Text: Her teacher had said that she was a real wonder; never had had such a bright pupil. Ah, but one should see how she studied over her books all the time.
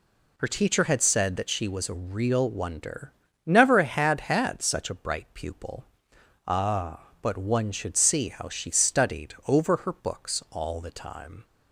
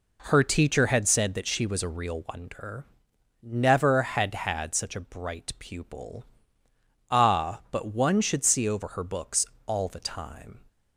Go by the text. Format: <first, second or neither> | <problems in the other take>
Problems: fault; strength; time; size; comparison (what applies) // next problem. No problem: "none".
first | skips "how she studied"; at 8.6 s // pauses between "books" and "all"; slight; at 9.4 s; 0.18 s long